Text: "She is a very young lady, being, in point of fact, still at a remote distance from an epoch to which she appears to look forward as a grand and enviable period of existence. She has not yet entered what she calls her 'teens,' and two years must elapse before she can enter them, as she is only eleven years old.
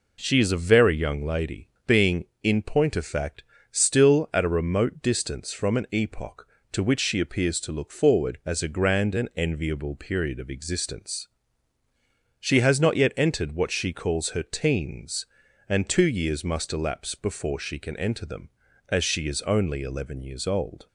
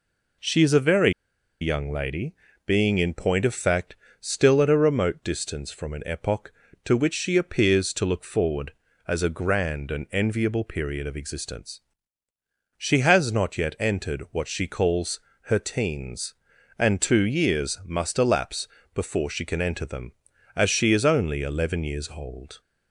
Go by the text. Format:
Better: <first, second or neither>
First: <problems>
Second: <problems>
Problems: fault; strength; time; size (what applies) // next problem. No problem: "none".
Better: first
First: none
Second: pauses between "very" and "young"; noticeable; at 1.1 s; 0.50 s long // pauses between "calls" and "her"; slight; at 15.1 s; 0.28 s long // pauses between "elapse" and "before"; slight; at 18.6 s; 0.26 s long